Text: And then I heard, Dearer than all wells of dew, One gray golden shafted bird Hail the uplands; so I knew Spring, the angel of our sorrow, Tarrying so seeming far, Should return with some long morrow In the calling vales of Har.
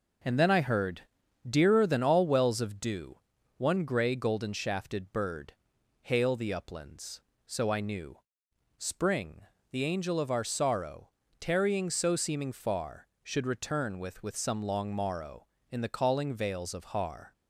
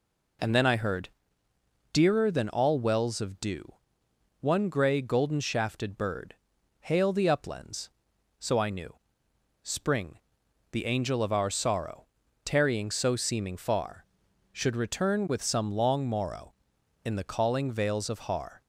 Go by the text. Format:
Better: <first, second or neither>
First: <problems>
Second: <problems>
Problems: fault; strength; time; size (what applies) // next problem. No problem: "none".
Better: second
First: pauses between "bird" and "Hail"; noticeable; at 5.5 s; 0.48 s long // pauses between "knew" and "Spring"; noticeable; at 8.1 s; 0.60 s long // says "with" twice; at 14.2 s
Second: pauses between "bird" and "Hail"; noticeable; at 6.3 s; 0.48 s long // pauses between "knew" and "Spring"; noticeable; at 8.9 s; 0.68 s long